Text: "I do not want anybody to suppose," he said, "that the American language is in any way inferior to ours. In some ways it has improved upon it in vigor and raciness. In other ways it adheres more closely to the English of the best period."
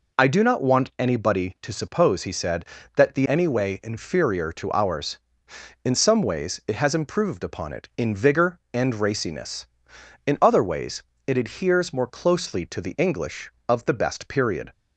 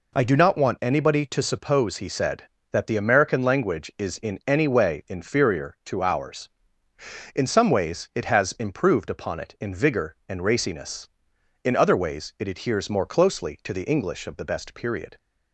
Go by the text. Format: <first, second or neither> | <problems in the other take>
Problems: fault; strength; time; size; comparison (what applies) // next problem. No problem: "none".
second | skips "American language is in"; at 3.2 s // pauses between "ways" and "it"; slight; at 11.0 s; 0.24 s long